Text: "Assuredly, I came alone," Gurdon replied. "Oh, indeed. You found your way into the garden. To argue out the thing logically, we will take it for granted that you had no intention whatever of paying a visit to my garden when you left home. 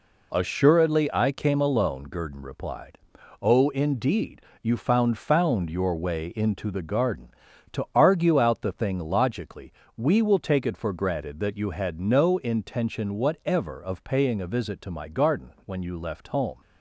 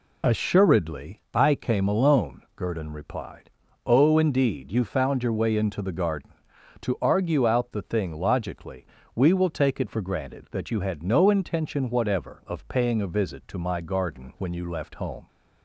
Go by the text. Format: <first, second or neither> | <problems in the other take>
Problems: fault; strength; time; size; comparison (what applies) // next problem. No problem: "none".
second | says "found" twice; at 5.1 s